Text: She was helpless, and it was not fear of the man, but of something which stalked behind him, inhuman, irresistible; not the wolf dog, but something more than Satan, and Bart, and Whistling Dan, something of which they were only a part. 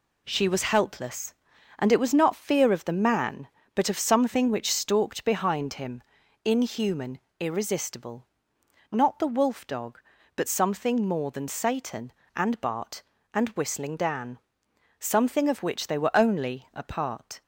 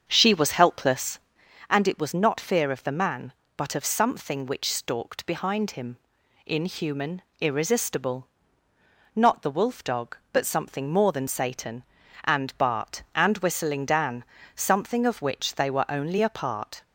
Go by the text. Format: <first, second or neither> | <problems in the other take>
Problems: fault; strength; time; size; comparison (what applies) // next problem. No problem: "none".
first | starts louder than the rest; strong; until 1.6 s; 7 dB